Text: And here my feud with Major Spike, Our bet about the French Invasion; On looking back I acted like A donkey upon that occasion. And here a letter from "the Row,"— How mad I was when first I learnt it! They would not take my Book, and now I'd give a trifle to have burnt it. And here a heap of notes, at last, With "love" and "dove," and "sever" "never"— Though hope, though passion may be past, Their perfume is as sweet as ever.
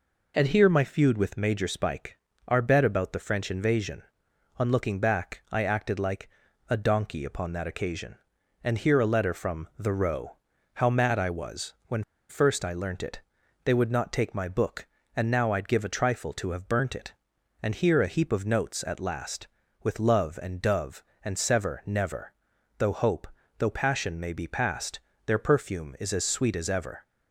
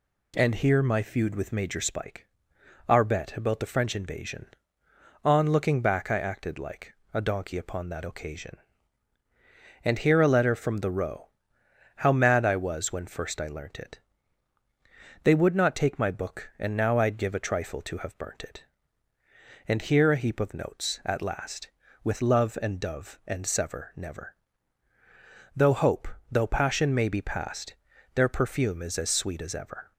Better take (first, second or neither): second